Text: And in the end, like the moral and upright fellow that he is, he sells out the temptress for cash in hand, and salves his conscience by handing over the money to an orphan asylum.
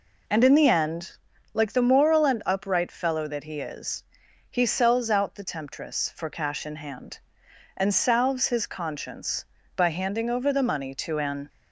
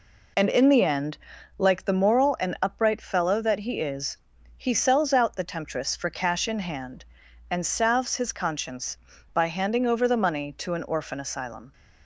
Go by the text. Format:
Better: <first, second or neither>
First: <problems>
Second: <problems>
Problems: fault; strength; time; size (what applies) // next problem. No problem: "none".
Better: second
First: stops before "orphan asylum"; at 11.4 s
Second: none